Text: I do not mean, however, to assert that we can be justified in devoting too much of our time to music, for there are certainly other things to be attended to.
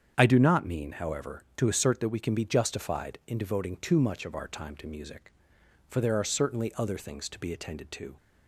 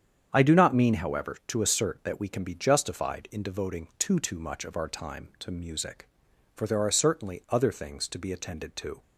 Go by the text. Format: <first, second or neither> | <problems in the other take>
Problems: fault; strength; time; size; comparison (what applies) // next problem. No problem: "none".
first | starts louder than the rest; strong; until 1.3 s; 8 dB; strong in the first // says "too" twice; at 4.1 s